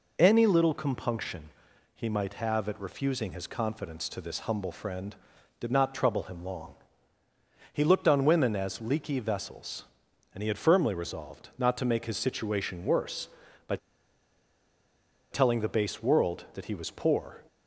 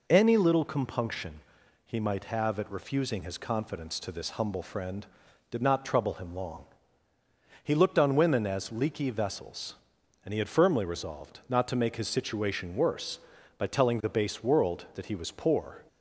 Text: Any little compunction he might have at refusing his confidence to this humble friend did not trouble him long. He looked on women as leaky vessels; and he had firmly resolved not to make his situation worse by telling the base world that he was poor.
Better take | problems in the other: second | pauses between "compunction" and "he"; at 1.5 s; 0.44 s long; also in the second // pauses between "by" and "telling"; strong; at 13.7 s; 1.5 s long

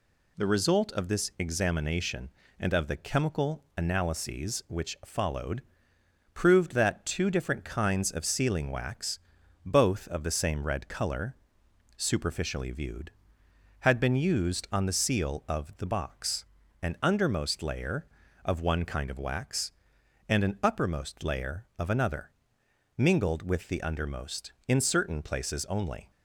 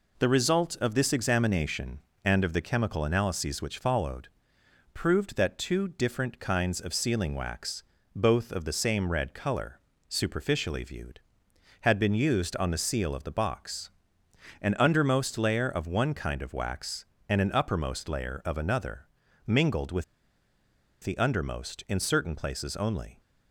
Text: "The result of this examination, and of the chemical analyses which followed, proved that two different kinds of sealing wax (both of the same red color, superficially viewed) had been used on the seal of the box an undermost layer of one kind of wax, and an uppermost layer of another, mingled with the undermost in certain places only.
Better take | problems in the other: first | pauses between "box" and "an"; noticeable; at 13.9 s; 0.72 s long; slight in the first // pauses between "with" and "the"; at 20.0 s; 0.99 s long

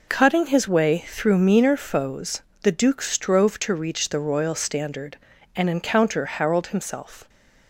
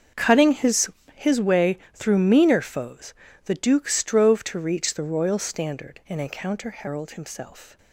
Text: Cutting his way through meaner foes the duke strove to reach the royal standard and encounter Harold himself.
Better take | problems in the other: first | starts louder than the rest; until 1.4 s; 6.5 dB // says "his" twice; at 1.1 s // pauses between "way" and "through"; slight; at 1.7 s; 0.18 s long // pauses between "foes" and "the"; slight; at 3.1 s; 0.32 s long; slight in the first

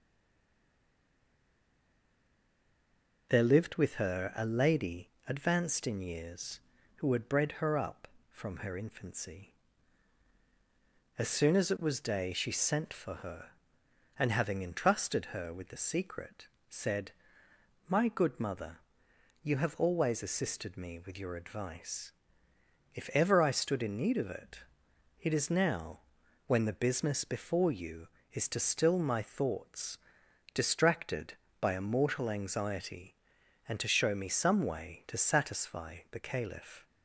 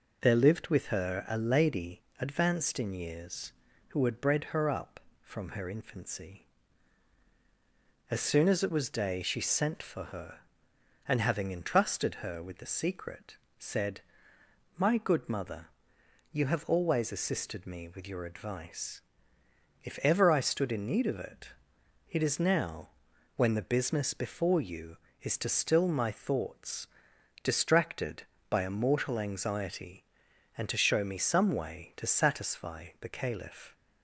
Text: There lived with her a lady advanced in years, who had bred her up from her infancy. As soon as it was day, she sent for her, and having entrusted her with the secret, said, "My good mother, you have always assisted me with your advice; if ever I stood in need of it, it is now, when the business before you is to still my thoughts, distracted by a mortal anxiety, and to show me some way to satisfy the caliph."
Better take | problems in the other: second | stays silent before the first word; strong; until 3.2 s; 3.2 s long // pauses between "lady" and "advanced"; slight; at 5.0 s; 0.18 s long; slight in the second

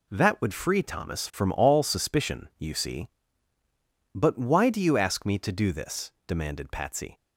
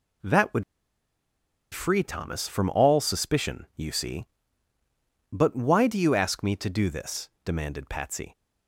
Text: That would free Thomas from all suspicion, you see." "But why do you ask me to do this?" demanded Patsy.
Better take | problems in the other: first | pauses between "would" and "free"; at 0.6 s; 1.1 s long

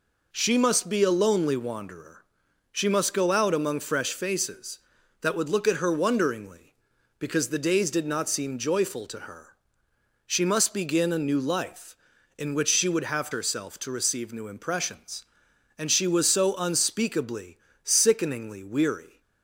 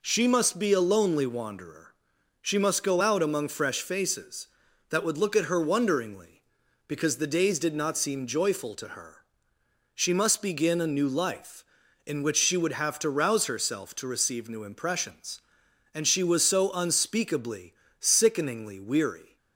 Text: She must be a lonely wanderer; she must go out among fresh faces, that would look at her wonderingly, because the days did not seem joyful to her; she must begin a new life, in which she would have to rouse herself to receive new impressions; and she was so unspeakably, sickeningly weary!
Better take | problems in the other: second | skips "to rouse"; at 13.3 s

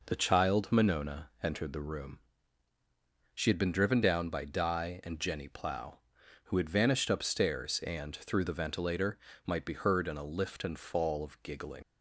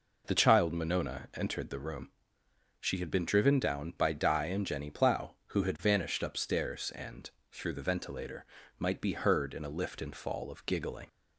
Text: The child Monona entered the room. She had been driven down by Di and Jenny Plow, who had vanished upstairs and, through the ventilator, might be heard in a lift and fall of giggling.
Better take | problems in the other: second | leaves "giggling" unfinished; at 11.8 s; 80 ms

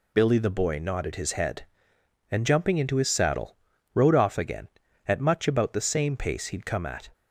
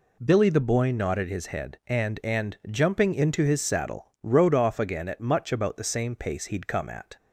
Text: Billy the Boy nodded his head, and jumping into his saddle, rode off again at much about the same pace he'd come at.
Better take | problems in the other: first | says "and" twice; at 2.2 s

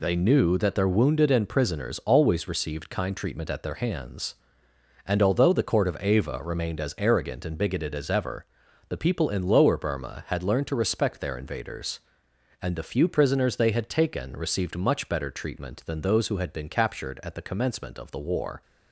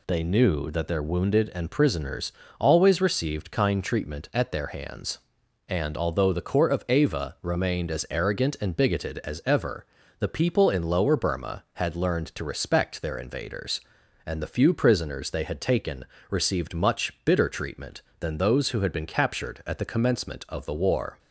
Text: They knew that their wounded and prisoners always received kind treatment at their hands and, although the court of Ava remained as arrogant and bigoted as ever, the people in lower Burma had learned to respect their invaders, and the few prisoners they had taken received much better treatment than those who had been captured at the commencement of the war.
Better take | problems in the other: first | pauses between "prisoners" and "always"; slight; at 2.3 s; 0.28 s long // pauses between "taken" and "received"; slight; at 16.0 s; 0.24 s long // says "bitter" for "better"; at 17.2 s

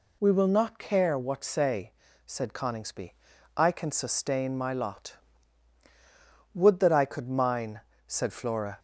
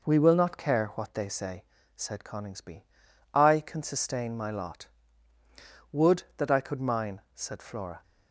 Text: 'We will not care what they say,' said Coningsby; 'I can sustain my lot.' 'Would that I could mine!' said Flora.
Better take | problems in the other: second | skips "they"; at 1.4 s

